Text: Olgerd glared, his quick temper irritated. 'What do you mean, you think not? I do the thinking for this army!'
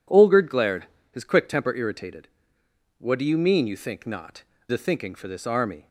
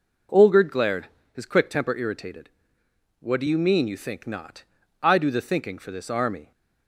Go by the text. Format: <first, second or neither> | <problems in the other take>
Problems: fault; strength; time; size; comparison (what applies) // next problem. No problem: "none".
second | skips "I do"; at 4.5 s